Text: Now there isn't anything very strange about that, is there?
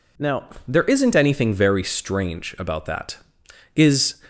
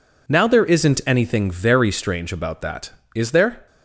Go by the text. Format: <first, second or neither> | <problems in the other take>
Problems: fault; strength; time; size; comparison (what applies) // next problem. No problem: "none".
second | pauses between "Now" and "there"; slight; at 0.4 s; 0.18 s long // stops before "there"; at 4.2 s